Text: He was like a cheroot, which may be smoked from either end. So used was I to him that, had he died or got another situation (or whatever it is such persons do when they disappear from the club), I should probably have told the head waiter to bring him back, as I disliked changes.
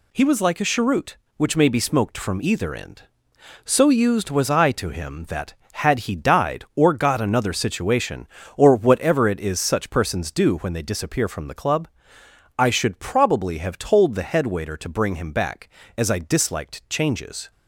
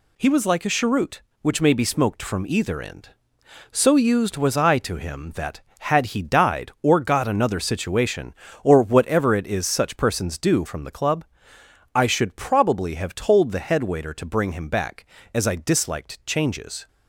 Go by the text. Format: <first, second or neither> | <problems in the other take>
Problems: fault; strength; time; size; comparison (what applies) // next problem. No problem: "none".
first | skips "when they disappear"; at 10.6 s